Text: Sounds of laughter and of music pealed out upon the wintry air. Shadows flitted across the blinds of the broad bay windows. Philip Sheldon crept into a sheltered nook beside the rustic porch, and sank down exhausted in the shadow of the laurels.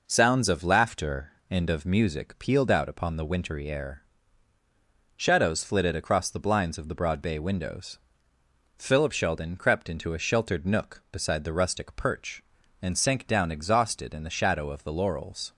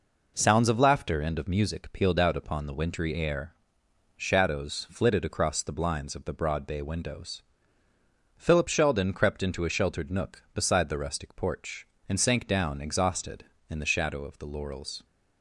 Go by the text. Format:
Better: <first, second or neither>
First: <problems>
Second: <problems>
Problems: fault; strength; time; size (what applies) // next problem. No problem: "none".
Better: second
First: says "perch" for "porch"; at 11.9 s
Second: none